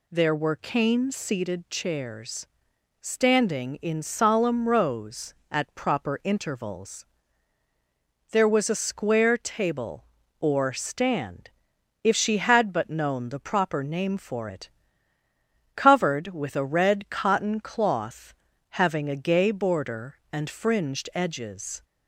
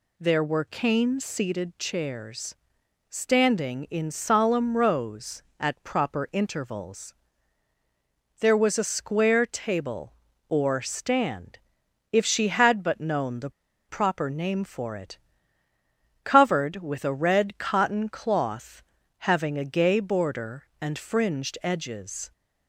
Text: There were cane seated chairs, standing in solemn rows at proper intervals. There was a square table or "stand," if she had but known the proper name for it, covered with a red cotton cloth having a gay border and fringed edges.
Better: first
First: pauses between "cloth" and "having"; at 18.3 s; 0.38 s long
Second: pauses between "the" and "proper"; at 13.5 s; 0.38 s long // pauses between "cloth" and "having"; at 18.8 s; 0.38 s long

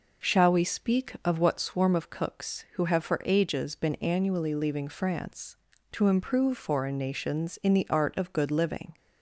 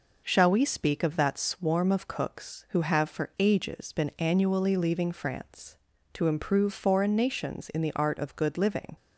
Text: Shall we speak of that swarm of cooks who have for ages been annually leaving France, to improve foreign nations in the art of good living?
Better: second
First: says "what" for "that"; at 1.3 s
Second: none

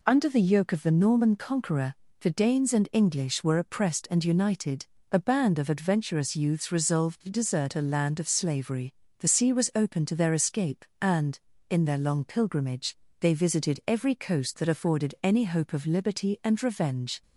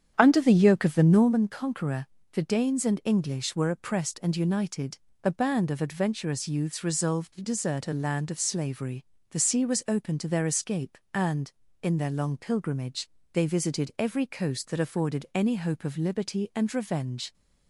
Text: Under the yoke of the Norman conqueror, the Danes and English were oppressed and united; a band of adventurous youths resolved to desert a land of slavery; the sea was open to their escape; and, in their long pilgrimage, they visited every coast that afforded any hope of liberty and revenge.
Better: first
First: none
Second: starts louder than the rest; strong; until 1.3 s; 8.5 dB

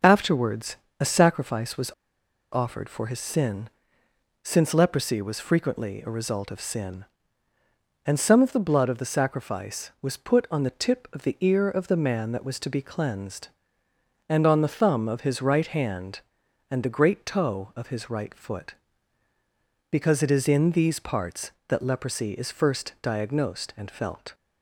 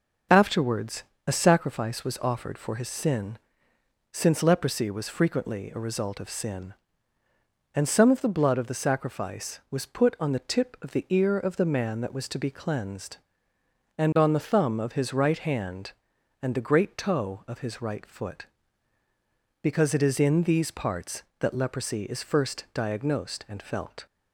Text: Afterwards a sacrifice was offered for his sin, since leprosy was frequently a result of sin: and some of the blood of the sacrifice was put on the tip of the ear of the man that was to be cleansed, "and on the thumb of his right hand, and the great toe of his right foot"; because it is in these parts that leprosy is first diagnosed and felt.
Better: second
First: starts louder than the rest; until 1.2 s; 6.5 dB // pauses between "Afterwards" and "a"; slight; at 0.7 s; 0.22 s long // pauses between "was" and "offered"; noticeable; at 1.9 s; 0.60 s long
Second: starts louder than the rest; until 1.5 s; 6 dB // pauses between "Afterwards" and "a"; slight; at 1.0 s; 0.22 s long

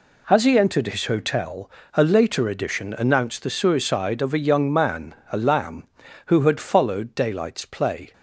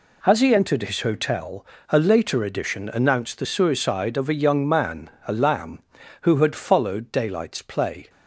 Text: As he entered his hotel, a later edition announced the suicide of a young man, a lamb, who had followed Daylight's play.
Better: neither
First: none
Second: none

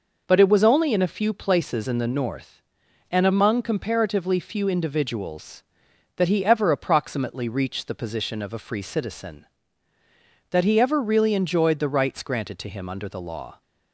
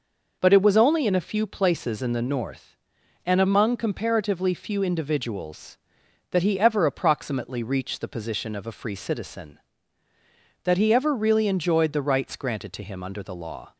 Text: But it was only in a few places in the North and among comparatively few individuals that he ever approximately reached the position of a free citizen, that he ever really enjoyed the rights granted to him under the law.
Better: neither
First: none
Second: none

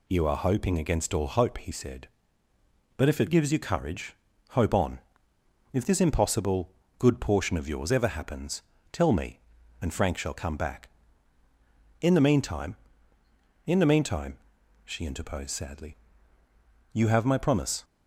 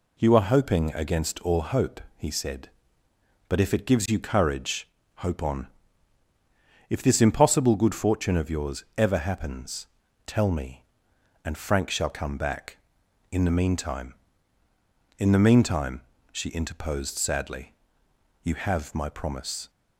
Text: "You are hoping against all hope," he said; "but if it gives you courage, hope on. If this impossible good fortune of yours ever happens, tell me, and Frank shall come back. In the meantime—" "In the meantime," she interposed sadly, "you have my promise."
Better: second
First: pauses between "impossible" and "good"; slight; at 6.7 s; 0.28 s long // says "portion" for "fortune"; at 7.2 s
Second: none

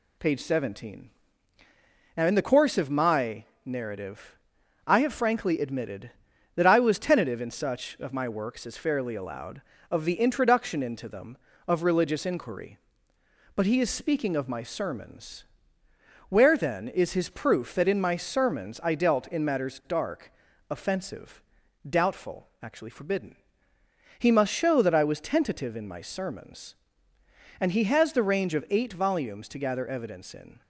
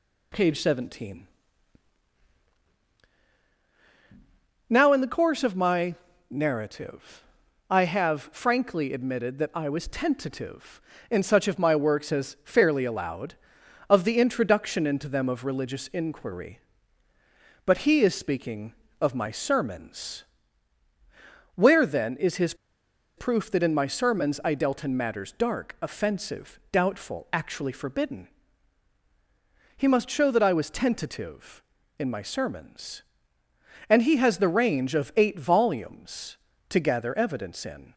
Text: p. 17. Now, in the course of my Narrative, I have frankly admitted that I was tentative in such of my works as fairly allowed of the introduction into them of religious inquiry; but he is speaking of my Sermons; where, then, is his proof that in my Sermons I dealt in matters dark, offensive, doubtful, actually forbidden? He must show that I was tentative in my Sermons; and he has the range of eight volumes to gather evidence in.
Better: first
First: pauses between "my" and "Narrative"; slight; at 3.4 s; 0.20 s long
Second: pauses between "my" and "Narrative"; slight; at 5.9 s; 0.36 s long // pauses between "his" and "proof"; noticeable; at 22.5 s; 0.62 s long

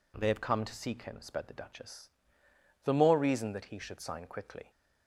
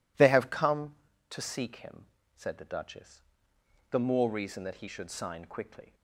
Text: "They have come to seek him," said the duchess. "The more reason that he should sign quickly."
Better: second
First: says "sped" for "said"; at 1.2 s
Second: none

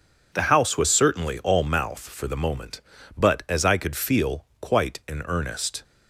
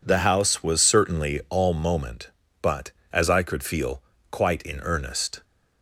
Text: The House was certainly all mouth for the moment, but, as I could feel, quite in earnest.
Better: first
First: none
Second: skips "mouth for the"; at 1.7 s

